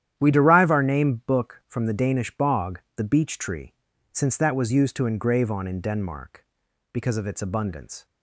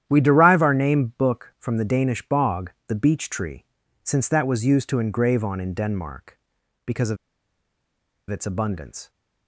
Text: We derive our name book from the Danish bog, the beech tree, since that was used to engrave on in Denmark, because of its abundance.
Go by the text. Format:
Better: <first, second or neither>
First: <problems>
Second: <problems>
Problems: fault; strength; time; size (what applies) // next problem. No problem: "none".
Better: first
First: starts louder than the rest; strong; until 1.2 s; 10.5 dB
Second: starts louder than the rest; strong; until 1.0 s; 10.5 dB // pauses between "of" and "its"; at 7.1 s; 1.1 s long